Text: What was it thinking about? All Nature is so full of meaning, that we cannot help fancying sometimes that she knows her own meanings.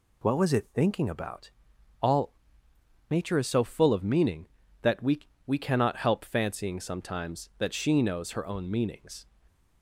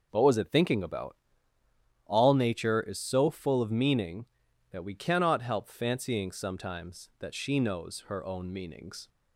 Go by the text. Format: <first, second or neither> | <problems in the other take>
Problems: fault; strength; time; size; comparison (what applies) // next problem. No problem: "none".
second | pauses between "All" and "Nature"; noticeable; at 2.3 s; 0.78 s long // says "we" twice; at 5.4 s